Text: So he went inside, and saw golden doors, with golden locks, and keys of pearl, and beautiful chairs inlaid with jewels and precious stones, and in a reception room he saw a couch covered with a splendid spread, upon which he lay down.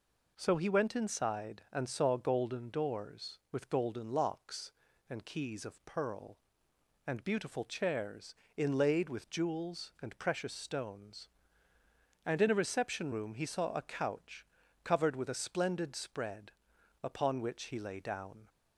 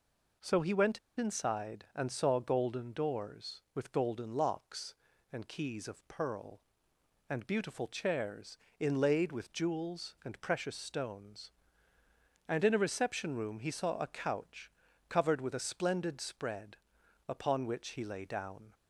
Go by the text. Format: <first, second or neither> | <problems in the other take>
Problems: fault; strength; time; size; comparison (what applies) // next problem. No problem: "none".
first | pauses between "went" and "inside"; slight; at 0.9 s; 0.18 s long // pauses between "chairs" and "inlaid"; slight; at 8.5 s; 0.22 s long; slight in the first // pauses between "couch" and "covered"; at 14.6 s; 0.40 s long; also in the first